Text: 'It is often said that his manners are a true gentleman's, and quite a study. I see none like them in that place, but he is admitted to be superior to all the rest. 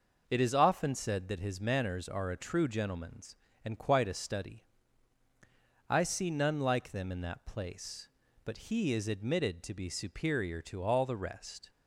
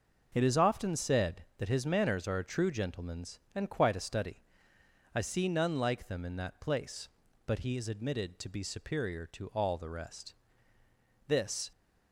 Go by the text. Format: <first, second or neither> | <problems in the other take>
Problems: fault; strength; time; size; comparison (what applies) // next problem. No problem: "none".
first | goes on to say "This"; slight; from 11.2 s on; 0.44 s long